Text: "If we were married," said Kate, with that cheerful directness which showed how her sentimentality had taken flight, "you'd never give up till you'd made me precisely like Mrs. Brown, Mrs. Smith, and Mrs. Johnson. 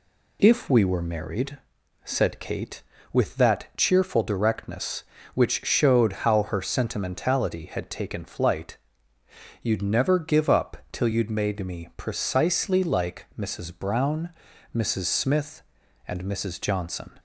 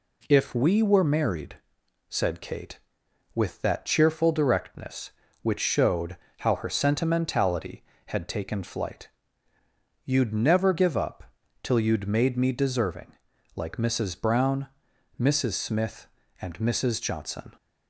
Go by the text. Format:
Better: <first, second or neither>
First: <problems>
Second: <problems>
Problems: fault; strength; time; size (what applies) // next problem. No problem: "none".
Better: first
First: pauses between "up" and "till"; slight; at 10.7 s; 0.16 s long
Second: pauses between "showed" and "how"; slight; at 6.1 s; 0.24 s long // pauses between "up" and "till"; at 11.2 s; 0.38 s long // says "deserving" for "precisely"; at 12.5 s